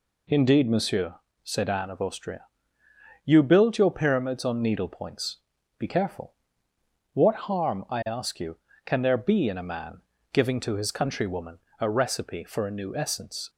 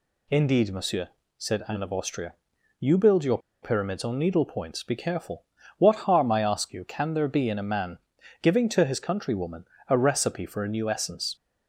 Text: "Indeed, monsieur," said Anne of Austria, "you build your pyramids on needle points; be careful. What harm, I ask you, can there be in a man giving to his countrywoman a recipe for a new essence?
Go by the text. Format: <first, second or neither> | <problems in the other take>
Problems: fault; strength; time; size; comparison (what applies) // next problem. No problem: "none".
first | pauses between "your" and "pyramids"; slight; at 3.3 s; 0.24 s long // pauses between "man" and "giving"; at 7.9 s; 0.44 s long; slight in the first // pauses between "countrywoman" and "a"; slight; at 9.6 s; 0.24 s long; slight in the first